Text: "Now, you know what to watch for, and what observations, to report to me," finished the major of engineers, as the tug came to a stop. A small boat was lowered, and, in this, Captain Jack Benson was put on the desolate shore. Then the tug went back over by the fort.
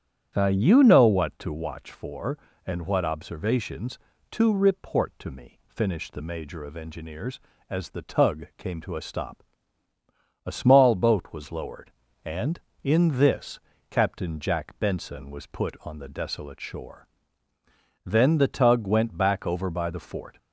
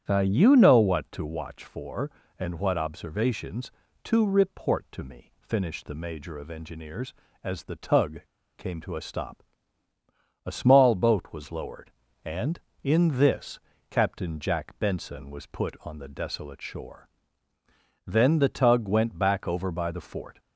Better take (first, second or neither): first